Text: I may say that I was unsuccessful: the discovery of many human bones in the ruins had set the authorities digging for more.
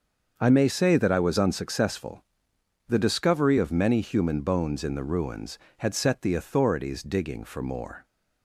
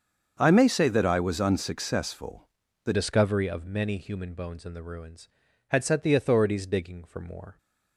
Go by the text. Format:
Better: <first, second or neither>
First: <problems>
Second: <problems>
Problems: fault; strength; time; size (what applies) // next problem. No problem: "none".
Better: first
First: starts louder than the rest; until 1.3 s; 6.5 dB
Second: starts louder than the rest; until 1.4 s; 7 dB // changes voice at "discovery"; from 2.9 s on; 4.6 s long